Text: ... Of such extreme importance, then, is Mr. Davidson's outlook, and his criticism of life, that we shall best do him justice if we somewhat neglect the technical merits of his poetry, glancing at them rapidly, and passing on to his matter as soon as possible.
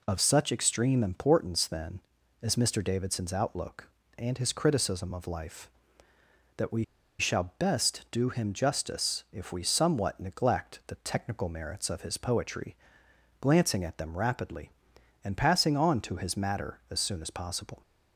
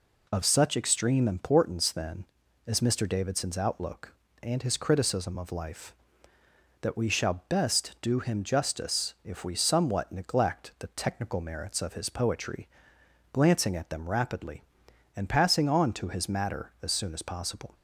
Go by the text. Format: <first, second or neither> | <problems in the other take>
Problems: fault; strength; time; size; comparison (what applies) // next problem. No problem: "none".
second | pauses between "we" and "shall"; slight; at 6.8 s; 0.35 s long